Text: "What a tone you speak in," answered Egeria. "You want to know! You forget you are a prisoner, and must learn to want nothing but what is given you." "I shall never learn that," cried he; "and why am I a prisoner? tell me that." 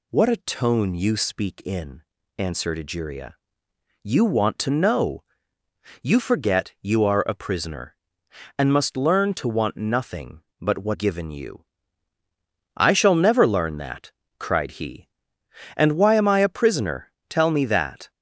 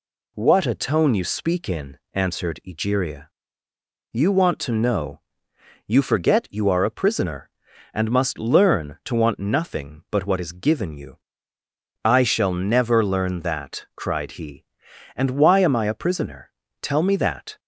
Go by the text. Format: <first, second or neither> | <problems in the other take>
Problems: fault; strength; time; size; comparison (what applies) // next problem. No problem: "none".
second | skips "is"; at 10.9 s